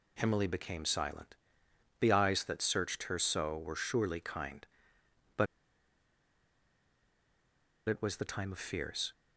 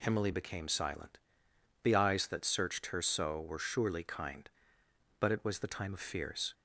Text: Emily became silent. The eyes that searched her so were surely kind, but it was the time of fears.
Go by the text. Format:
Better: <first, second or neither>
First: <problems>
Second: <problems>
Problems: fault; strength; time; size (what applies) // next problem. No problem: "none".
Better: second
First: pauses between "but" and "it"; strong; at 5.4 s; 2.4 s long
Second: none